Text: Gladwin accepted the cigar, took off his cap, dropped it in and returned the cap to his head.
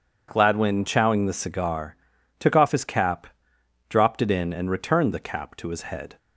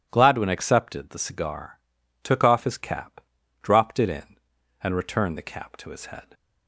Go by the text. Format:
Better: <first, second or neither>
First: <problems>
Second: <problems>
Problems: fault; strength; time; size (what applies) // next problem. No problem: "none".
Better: second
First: says "chowing" for "accepted"; at 0.8 s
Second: none